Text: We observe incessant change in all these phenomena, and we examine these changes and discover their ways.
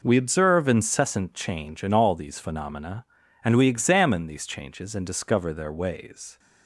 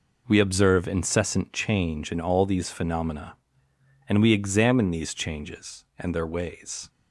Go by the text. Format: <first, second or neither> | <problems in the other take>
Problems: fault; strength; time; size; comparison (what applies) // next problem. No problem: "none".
first | skips "discover"; at 6.1 s